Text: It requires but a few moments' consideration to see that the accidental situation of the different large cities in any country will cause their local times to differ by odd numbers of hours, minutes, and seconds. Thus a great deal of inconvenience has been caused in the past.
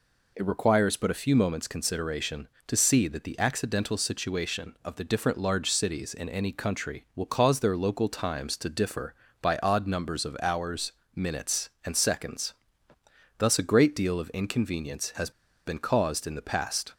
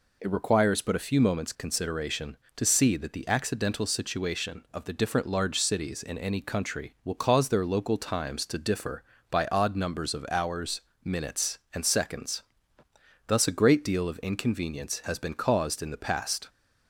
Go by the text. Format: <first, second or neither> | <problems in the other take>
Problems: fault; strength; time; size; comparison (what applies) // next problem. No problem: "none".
second | pauses between "has" and "been"; slight; at 15.3 s; 0.35 s long